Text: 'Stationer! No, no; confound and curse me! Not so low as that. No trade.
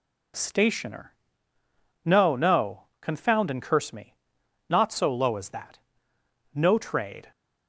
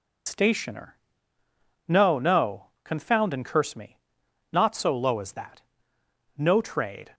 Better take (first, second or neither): first